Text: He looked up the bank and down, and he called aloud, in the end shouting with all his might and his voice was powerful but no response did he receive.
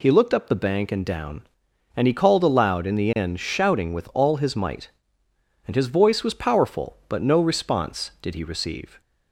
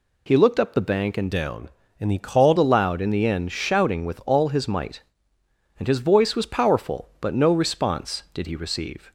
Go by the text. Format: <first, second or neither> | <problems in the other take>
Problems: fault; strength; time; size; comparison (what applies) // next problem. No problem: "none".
first | changes voice from "down" to "called"; from 1.3 to 2.5 s; 1.2 s long